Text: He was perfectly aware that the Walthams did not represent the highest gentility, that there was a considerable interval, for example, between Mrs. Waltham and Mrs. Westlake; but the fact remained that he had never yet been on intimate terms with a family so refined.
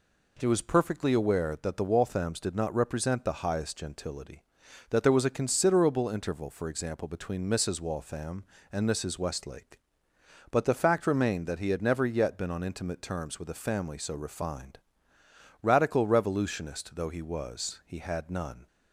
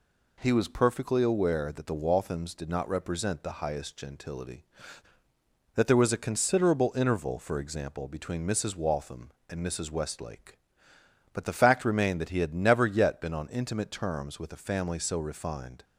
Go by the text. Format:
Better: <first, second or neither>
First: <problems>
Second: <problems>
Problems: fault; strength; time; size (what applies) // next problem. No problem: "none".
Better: second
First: goes on to say "Radical revolutionist though he was he had none"; strong; from 15.6 s on; 3.0 s long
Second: none